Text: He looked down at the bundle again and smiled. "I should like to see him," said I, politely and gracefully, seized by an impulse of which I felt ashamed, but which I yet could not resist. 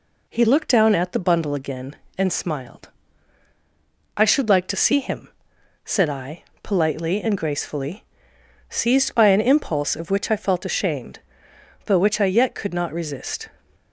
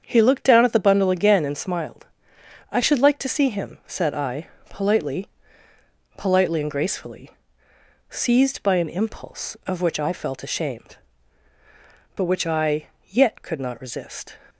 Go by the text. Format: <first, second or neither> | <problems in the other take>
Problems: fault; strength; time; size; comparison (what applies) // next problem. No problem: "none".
first | starts louder than the rest; strong; until 1.0 s; 7.5 dB // says "politely" twice; at 6.1 s // pauses between "I" and "yet"; slight; at 12.8 s; 0.20 s long